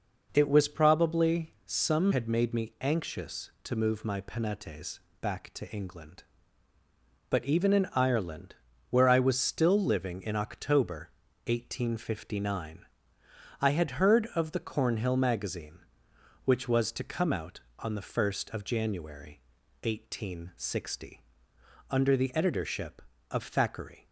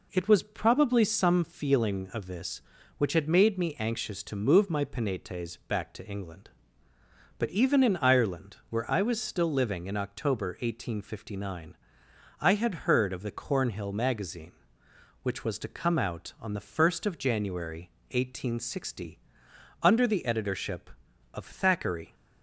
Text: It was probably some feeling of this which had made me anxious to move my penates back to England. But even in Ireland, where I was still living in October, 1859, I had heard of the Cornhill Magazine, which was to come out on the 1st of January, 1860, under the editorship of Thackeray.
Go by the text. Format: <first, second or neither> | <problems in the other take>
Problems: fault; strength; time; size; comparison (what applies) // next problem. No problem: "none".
second | skips "feeling of this which"; at 2.1 s // pauses between "penates" and "back"; slight; at 4.9 s; 0.22 s long